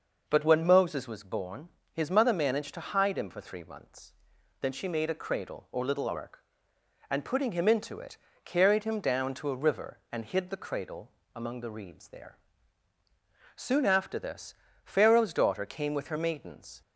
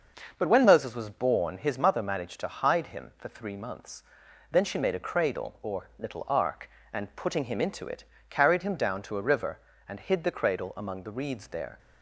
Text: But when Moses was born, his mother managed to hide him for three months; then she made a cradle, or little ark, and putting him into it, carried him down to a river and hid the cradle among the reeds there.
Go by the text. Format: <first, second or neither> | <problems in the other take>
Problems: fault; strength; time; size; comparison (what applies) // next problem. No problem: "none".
second | pauses between "cradle" and "among"; slight; at 11.1 s; 0.20 s long // goes on to say "Soon after this Pharaoh's daughter came with her maidens"; strong; from 13.5 s on; 3.2 s long